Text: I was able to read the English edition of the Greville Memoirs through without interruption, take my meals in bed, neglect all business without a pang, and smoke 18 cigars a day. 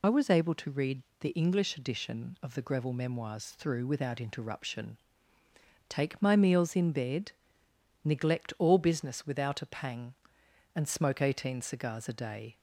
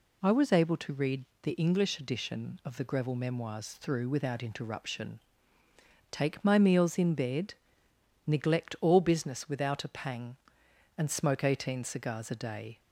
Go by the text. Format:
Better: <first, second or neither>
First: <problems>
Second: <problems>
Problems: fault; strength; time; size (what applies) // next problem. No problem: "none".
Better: second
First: loses the start of "I"; at 0.0 s; 45 ms // pauses between "read" and "the"; slight; at 1.0 s; 0.18 s long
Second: pauses between "read" and "the"; slight; at 1.2 s; 0.18 s long